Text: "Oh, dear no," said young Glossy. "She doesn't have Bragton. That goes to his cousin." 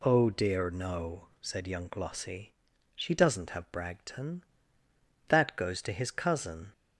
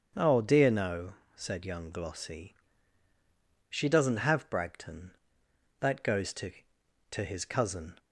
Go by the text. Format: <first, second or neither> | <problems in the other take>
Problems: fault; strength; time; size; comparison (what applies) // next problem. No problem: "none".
first | starts louder than the rest; until 1.3 s; 7 dB // says "to" twice; at 7.1 s